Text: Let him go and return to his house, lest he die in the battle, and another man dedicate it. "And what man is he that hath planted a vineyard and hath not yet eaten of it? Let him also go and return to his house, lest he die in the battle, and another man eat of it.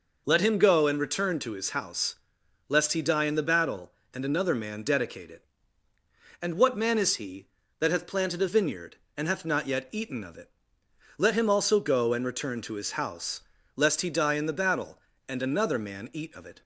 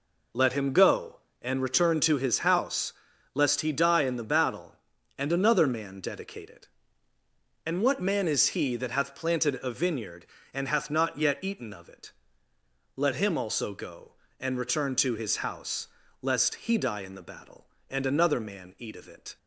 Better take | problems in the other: neither | none

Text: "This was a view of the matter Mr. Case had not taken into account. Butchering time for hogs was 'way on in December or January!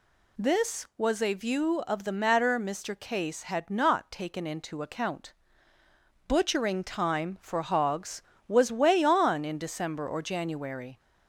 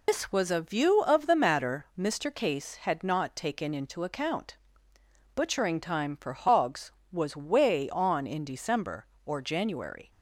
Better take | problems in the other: first | loses the start of "This"; at 0.0 s; 115 ms

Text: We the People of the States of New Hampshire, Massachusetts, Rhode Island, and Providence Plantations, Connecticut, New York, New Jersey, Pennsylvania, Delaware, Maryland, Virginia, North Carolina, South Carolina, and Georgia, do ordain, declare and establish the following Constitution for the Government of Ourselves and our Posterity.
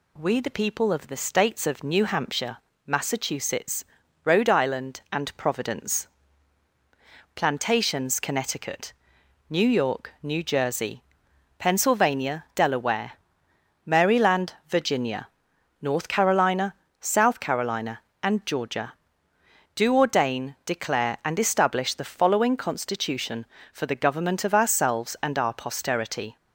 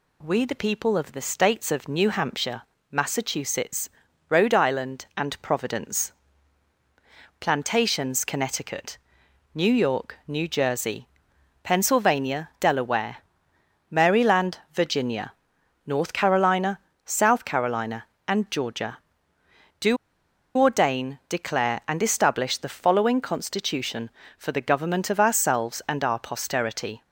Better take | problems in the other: first | pauses between "Providence" and "Plantations"; strong; at 6.1 s; 1.2 s long; strong in the first // pauses between "do" and "ordain"; noticeable; at 19.9 s; 0.61 s long

